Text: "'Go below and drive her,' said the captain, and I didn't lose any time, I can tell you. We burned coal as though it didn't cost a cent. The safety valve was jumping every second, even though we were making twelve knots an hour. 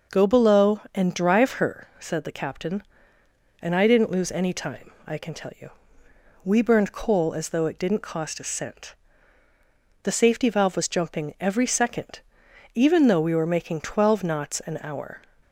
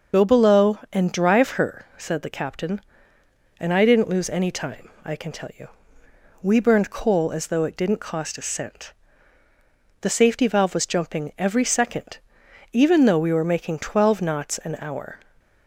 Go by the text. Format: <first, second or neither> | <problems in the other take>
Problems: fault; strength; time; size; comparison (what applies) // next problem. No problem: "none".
first | loses the start of "Go"; at 0.1 s; 50 ms // starts louder than the rest; noticeable; until 1.2 s; 6 dB